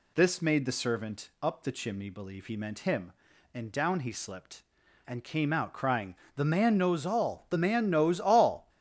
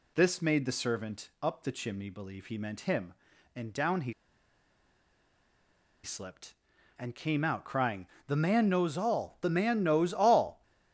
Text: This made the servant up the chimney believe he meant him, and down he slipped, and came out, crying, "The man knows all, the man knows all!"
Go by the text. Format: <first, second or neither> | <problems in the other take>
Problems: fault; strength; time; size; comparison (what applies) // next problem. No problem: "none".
first | pauses between "he" and "slipped"; strong; at 4.1 s; 1.9 s long